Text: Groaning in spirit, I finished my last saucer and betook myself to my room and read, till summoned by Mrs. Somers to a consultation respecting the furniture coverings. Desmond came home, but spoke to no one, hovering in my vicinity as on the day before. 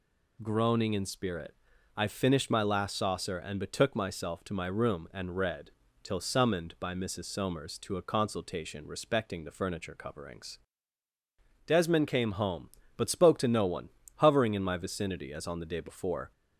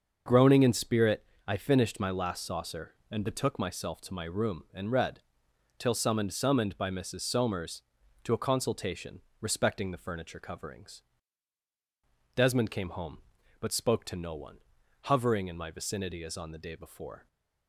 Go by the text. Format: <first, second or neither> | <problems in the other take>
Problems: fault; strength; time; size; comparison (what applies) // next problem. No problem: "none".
first | starts louder than the rest; until 1.5 s; 6.5 dB // says "summoned" twice; at 6.3 s // pauses between "consultation" and "respecting"; slight; at 9.2 s; 0.18 s long